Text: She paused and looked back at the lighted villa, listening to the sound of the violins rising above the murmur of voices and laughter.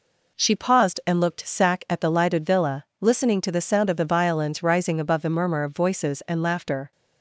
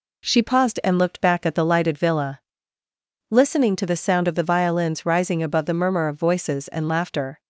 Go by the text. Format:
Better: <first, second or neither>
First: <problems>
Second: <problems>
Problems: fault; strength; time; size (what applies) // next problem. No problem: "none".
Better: second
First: says "sack" for "back"; at 1.4 s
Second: none